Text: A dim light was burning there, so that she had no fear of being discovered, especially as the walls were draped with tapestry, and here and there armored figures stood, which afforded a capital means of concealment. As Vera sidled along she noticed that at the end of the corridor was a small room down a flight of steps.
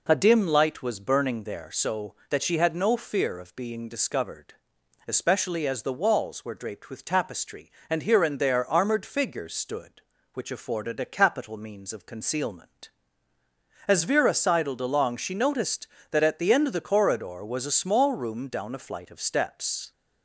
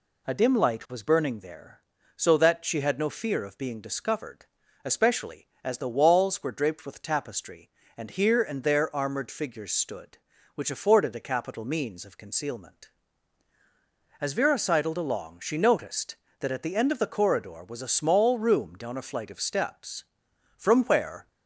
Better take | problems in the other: first | goes on to say "From where"; noticeable; from 20.5 s on; 0.72 s long

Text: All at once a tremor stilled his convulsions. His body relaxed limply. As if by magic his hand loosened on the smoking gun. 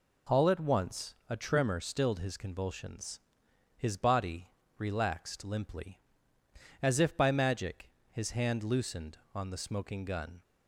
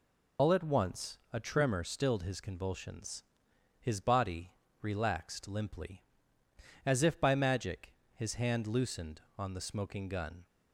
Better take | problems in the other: first | loses the start of "All"; at 0.3 s; 95 ms // pauses between "once" and "a"; slight; at 1.1 s; 0.16 s long; slight in the first // pauses between "body" and "relaxed"; slight; at 4.5 s; 0.28 s long; slight in the first // pauses between "magic" and "his"; slight; at 7.9 s; 0.22 s long; slight in the first

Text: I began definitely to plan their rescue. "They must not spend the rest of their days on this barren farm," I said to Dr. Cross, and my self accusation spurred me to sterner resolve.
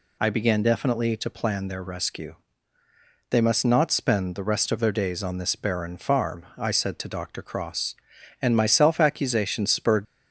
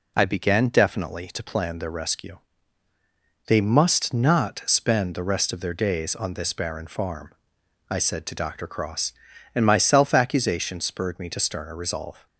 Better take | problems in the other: second | stops before "me to sterner resolve"; at 10.0 s

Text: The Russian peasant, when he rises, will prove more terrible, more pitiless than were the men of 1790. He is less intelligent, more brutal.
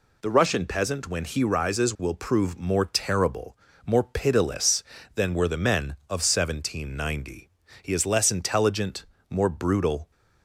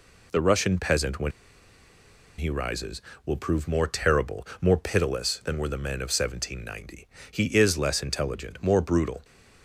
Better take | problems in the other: first | pauses between "when" and "he"; at 1.3 s; 1.0 s long

